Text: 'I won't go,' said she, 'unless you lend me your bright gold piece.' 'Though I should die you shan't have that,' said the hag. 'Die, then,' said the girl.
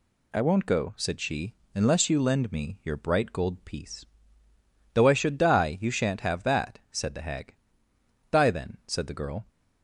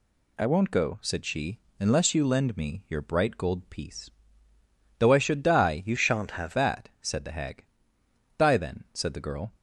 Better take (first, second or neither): first